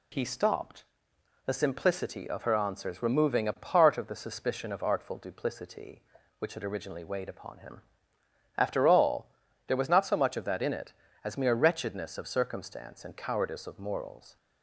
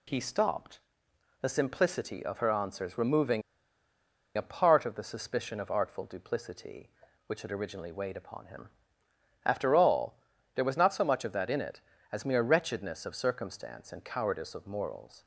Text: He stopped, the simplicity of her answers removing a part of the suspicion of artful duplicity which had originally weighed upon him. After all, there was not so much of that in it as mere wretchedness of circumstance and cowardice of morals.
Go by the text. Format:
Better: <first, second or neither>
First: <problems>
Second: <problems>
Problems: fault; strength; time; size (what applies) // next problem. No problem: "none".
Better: first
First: none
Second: pauses between "removing" and "a"; noticeable; at 3.4 s; 0.94 s long